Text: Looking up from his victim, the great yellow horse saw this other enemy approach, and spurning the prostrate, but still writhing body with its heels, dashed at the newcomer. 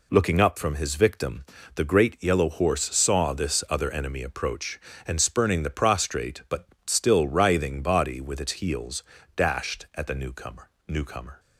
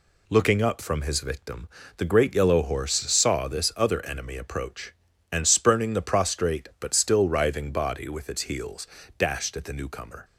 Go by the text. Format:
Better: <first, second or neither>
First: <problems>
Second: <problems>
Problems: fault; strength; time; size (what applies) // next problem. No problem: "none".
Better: second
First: pauses between "but" and "still"; slight; at 6.6 s; 0.22 s long // says "newcomer" twice; at 10.8 s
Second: none